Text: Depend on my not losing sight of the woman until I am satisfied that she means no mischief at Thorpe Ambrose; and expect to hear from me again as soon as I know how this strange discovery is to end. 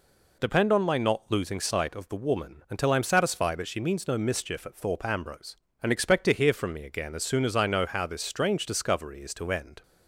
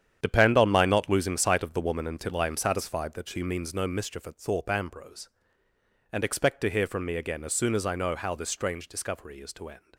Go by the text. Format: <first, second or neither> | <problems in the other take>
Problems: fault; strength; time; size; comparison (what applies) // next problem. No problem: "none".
first | gets quieter; strong; throughout; 10.5 dB